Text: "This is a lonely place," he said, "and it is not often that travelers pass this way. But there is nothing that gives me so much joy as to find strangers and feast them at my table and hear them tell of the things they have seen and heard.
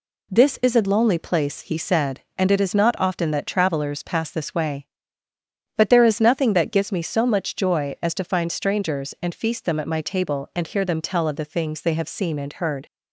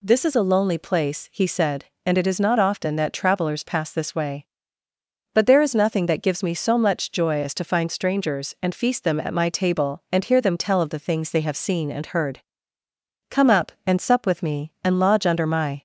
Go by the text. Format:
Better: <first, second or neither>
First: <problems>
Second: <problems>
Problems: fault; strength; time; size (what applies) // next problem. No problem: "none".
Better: first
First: none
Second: goes on to say "Come up and sup with me and lodge under my"; strong; from 13.2 s on; 2.5 s long